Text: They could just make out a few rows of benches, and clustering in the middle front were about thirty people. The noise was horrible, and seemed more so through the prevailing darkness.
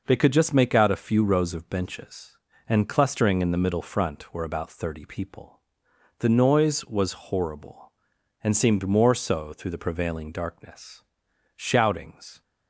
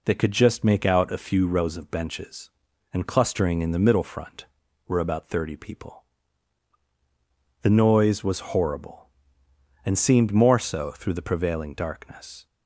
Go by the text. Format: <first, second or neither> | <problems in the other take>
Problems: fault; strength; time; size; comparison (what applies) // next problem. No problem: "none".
second | goes on to say "Shoutings"; noticeable; from 11.5 s on; 0.86 s long